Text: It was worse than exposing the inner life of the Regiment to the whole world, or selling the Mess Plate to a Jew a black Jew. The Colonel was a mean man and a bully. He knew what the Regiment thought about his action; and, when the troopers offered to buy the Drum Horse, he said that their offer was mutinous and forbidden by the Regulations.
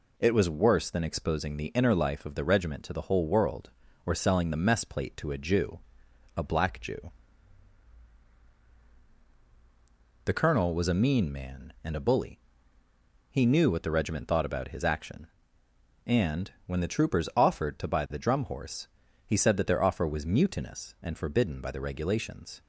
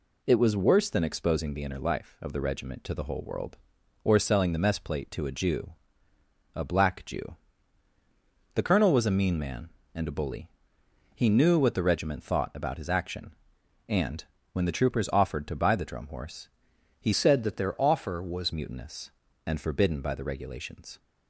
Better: first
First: pauses between "Jew" and "a"; noticeable; at 5.7 s; 0.58 s long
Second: pauses between "Jew" and "a"; noticeable; at 5.7 s; 0.82 s long // changes voice from "said" to "was"; from 17.1 to 18.5 s; 1.4 s long

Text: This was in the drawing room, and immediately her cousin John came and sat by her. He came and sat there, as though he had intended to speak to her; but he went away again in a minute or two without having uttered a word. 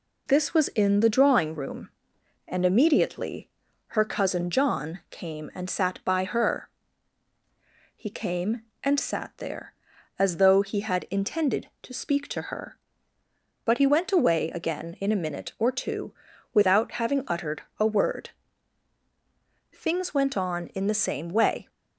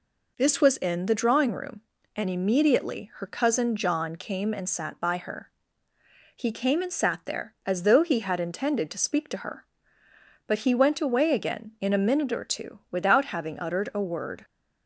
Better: second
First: pauses between "immediately" and "her"; at 3.4 s; 0.40 s long // pauses between "two" and "without"; at 16.1 s; 0.40 s long // pauses between "uttered" and "a"; slight; at 17.6 s; 0.16 s long // goes on to say "Things went on in the same way"; strong; from 19.7 s on; 1.9 s long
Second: none

